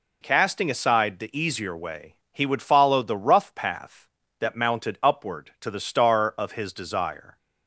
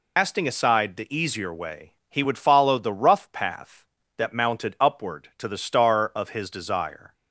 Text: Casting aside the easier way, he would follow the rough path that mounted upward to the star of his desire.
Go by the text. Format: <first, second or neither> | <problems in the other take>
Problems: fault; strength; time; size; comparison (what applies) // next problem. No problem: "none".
first | loses the start of "Casting"; at 0.1 s; 170 ms